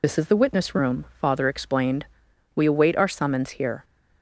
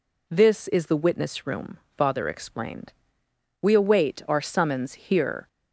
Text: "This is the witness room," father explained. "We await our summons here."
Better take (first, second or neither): second